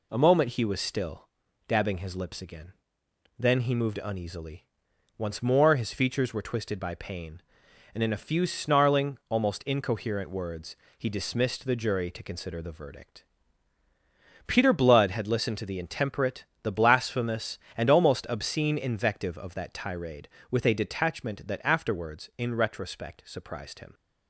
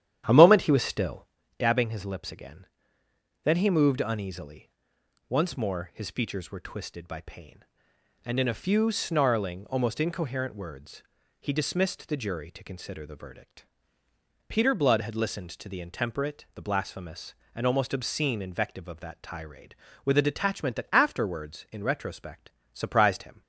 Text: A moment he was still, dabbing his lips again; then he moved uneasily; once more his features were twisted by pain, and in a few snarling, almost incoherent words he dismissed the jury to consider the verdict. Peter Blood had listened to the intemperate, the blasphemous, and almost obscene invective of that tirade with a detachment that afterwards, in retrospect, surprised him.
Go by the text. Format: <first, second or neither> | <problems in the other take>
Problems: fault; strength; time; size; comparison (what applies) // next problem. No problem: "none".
first | starts louder than the rest; strong; until 1.5 s; 10.5 dB // pauses between "words" and "he"; at 11.0 s; 0.38 s long; slight in the first